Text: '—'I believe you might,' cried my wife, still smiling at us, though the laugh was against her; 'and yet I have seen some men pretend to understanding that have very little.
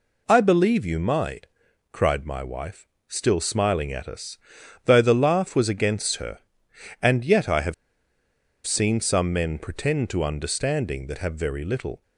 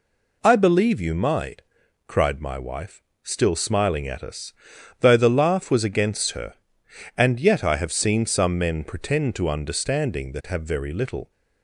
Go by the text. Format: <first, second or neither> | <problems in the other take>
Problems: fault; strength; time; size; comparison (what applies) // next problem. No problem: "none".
second | pauses between "have" and "seen"; noticeable; at 7.7 s; 0.91 s long